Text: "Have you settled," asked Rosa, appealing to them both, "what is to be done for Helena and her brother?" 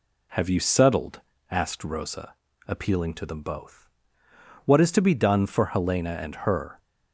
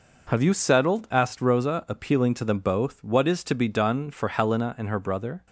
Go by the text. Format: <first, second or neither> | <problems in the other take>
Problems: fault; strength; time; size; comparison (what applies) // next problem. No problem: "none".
second | stops before "brother"; at 6.7 s